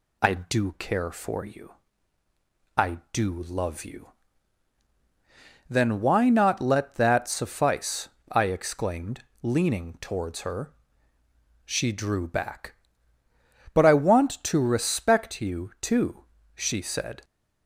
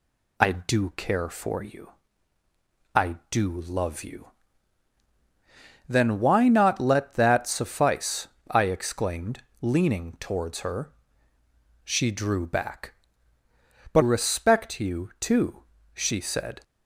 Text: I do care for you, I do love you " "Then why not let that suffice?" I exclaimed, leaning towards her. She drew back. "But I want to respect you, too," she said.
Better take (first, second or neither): first